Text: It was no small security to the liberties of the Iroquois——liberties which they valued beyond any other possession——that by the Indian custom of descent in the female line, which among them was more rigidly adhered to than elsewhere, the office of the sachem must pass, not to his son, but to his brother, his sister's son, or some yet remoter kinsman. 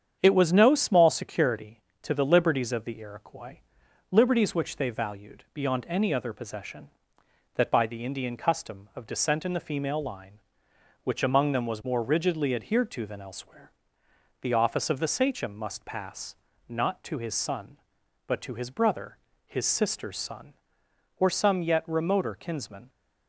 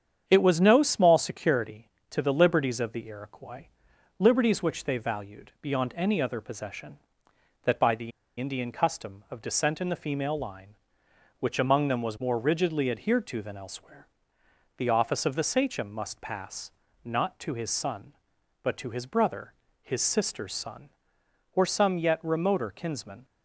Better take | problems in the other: first | starts louder than the rest; strong; until 1.2 s; 8 dB; strong in the first // pauses between "the" and "Indian"; slight; at 8.1 s; 0.27 s long

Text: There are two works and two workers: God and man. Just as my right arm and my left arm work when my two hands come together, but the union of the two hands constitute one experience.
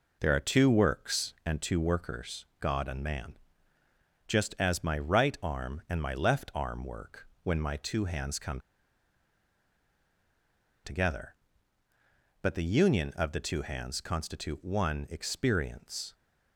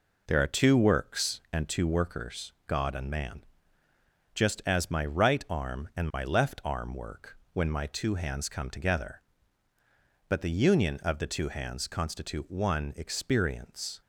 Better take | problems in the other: second | pauses between "work" and "when"; slight; at 7.2 s; 0.16 s long; slight in the second // pauses between "come" and "together"; strong; at 8.5 s; 2.2 s long

